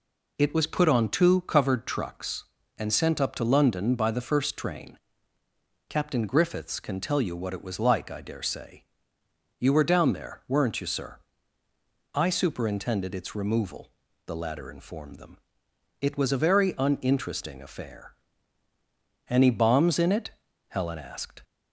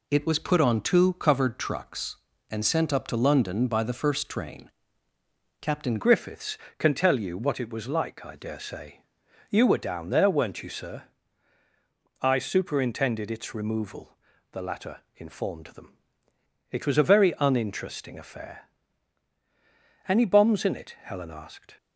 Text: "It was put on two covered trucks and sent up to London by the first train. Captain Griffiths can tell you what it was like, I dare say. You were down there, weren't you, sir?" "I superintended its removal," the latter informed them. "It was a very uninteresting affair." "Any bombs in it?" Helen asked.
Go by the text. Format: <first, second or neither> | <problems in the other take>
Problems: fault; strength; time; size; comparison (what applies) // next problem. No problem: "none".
first | changes voice at "Griffiths"; from 5.9 s on; 15.8 s long